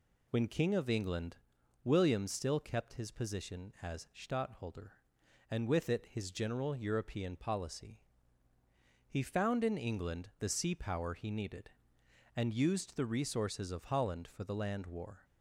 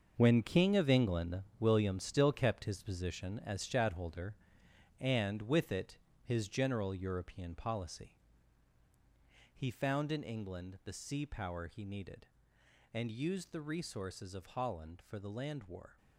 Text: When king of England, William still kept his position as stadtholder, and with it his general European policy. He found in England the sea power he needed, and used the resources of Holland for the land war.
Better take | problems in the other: first | gets quieter; strong; throughout; 11 dB // pauses between "it" and "his"; slight; at 5.9 s; 0.24 s long

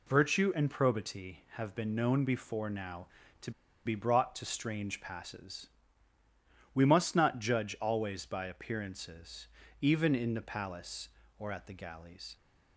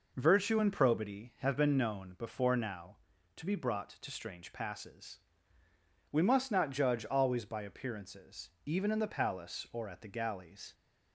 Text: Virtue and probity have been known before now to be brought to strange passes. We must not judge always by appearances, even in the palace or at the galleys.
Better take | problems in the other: second | pauses between "to" and "be"; slight; at 3.5 s; 0.34 s long

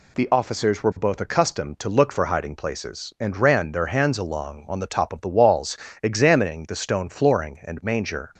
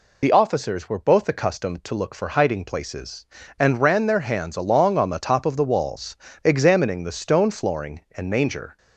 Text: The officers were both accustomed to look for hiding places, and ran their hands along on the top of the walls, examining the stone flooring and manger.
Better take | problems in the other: first | loses the start of "The"; at 0.2 s; 30 ms

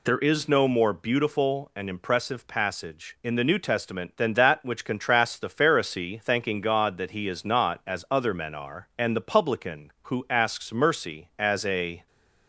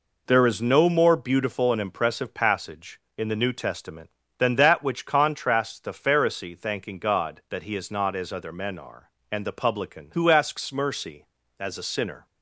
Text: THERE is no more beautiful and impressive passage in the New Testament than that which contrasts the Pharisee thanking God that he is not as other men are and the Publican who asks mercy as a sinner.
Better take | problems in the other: second | stops before "sinner"; at 12.0 s

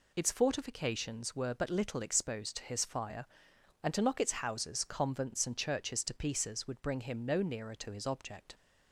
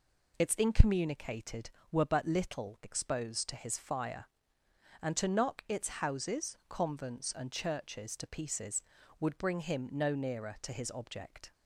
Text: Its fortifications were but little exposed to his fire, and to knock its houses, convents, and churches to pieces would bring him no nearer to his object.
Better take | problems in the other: first | says "incommunicated" for "fortifications"; at 0.5 s

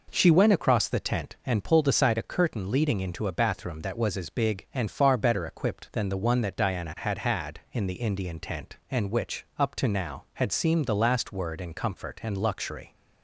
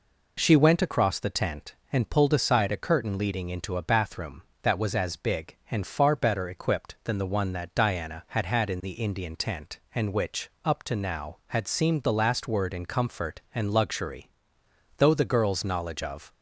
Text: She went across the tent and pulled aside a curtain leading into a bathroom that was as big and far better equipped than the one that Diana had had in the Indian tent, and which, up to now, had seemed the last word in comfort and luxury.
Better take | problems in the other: first | goes on to say "Though the girl's knowledge of"; from 14.9 s on; 1.3 s long

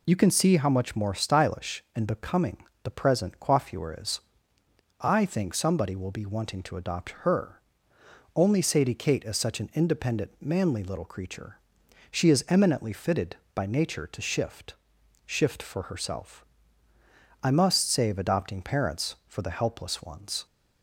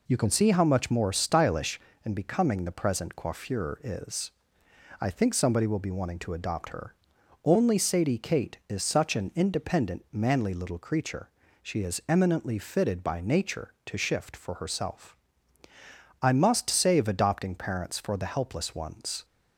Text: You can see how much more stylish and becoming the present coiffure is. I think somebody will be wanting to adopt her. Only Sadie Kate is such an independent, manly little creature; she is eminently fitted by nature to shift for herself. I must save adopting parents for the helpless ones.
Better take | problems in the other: second | pauses between "becoming" and "the"; slight; at 2.5 s; 0.26 s long // says "shift" twice; at 15.2 s

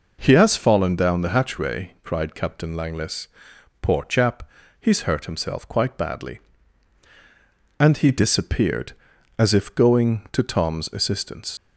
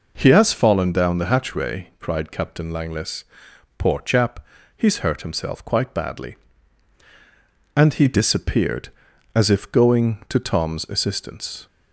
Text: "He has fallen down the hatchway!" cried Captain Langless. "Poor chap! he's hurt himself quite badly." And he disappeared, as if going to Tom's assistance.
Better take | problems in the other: second | leaves "assistance" unfinished; at 11.5 s; 125 ms

